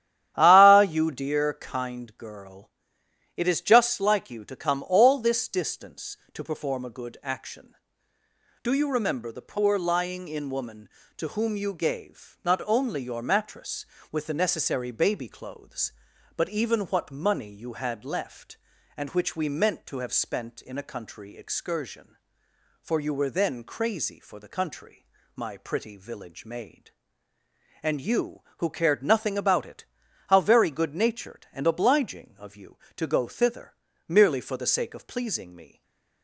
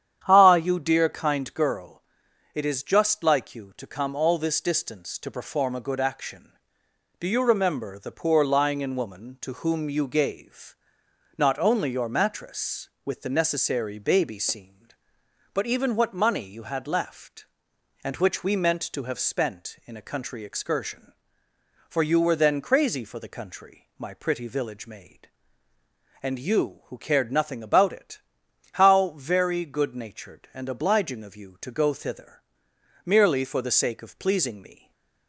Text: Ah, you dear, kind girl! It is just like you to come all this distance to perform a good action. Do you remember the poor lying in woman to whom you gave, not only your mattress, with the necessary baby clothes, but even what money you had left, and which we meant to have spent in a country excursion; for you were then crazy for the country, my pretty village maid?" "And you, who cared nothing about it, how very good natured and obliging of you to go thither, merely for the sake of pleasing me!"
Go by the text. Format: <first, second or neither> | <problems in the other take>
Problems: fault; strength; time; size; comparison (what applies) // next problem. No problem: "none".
first | starts louder than the rest; strong; until 1.2 s; 9.5 dB; strong in the first // says "seemed" for "clothes"; at 14.3 s // stays silent after the last word; slight; from 34.7 s on; 0.5 s long; slight in the first